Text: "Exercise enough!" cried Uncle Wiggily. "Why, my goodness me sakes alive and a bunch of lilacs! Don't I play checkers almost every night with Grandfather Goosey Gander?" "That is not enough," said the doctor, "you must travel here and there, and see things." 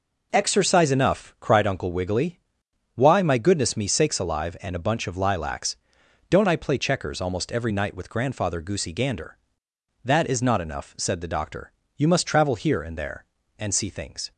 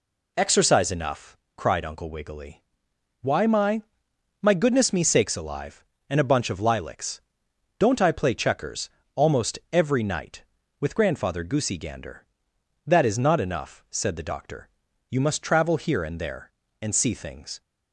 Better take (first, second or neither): first